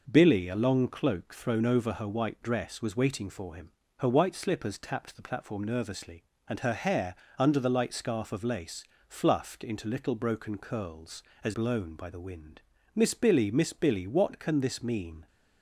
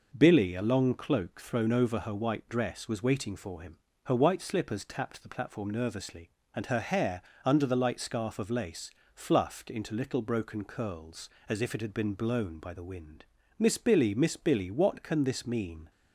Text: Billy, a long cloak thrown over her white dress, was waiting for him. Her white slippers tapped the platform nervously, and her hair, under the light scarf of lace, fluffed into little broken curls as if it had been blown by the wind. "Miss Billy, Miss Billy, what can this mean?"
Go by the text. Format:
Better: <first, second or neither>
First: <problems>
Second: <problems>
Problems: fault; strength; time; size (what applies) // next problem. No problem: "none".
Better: second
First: skips "if it had been"; at 11.5 s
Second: none